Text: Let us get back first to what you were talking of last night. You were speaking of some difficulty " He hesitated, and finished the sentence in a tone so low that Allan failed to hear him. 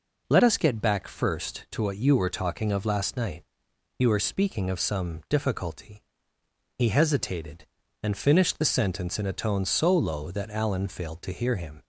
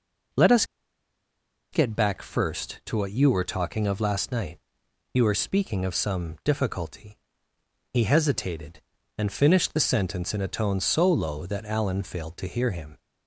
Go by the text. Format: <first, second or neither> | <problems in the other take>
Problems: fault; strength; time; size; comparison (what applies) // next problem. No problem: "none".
first | pauses between "us" and "get"; at 0.6 s; 1.0 s long